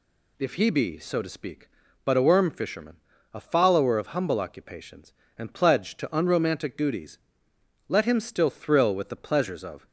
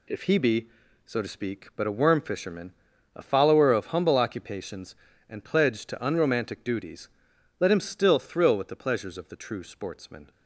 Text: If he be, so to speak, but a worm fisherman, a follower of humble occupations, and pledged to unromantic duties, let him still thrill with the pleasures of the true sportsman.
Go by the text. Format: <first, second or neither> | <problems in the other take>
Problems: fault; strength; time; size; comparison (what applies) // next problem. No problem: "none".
second | stops before "the true sportsman"; at 9.8 s